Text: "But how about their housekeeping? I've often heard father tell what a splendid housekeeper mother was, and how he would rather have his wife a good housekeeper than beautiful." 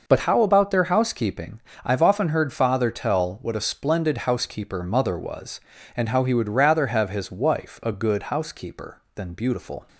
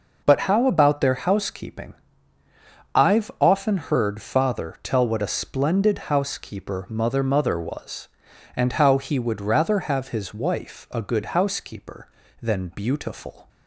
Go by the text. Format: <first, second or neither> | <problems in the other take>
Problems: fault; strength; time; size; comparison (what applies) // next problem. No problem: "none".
first | says "mother" twice; at 7.2 s